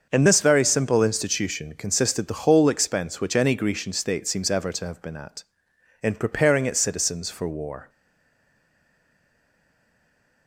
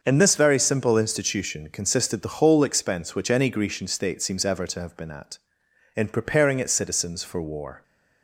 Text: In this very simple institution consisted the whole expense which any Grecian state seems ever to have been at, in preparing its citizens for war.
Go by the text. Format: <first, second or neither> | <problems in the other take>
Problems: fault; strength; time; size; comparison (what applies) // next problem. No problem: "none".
second | starts louder than the rest; until 1.1 s; 6.5 dB; also in the second // stays silent after the last word; strong; from 7.8 s on; 2.6 s long